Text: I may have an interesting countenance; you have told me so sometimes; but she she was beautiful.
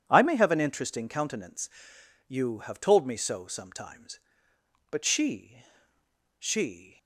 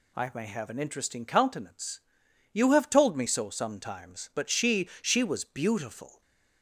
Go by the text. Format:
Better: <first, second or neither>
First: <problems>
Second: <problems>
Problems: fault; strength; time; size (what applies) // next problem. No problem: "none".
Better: second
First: pauses between "she" and "she"; noticeable; at 5.6 s; 0.75 s long // stops before "was beautiful"; at 6.9 s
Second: none